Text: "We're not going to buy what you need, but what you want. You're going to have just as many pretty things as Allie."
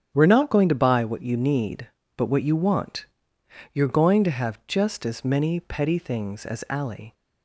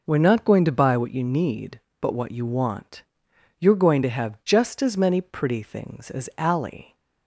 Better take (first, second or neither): second